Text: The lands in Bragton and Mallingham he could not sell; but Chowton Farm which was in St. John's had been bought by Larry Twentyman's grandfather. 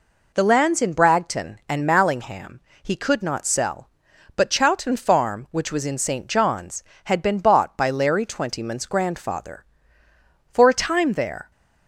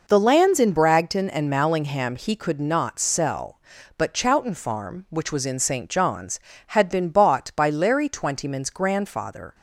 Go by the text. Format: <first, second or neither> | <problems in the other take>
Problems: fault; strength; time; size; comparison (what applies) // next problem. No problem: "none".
second | pauses between "Mallingham" and "he"; slight; at 2.6 s; 0.22 s long // goes on to say "For a time there"; noticeable; from 10.5 s on; 1.0 s long